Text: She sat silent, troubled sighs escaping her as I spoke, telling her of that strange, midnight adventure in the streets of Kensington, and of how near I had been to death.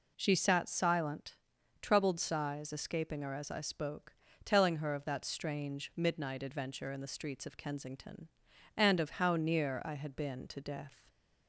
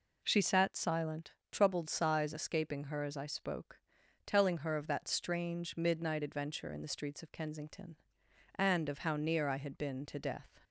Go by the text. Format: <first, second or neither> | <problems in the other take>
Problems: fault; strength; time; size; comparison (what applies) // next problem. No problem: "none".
neither | none